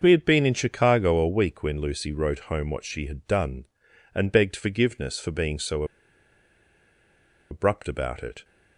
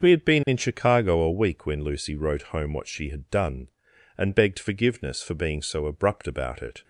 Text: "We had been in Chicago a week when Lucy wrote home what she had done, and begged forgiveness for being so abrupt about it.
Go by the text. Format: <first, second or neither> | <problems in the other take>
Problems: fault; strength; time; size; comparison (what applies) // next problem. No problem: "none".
second | starts louder than the rest; until 1.0 s; 6.5 dB; also in the second // pauses between "so" and "abrupt"; strong; at 5.8 s; 1.6 s long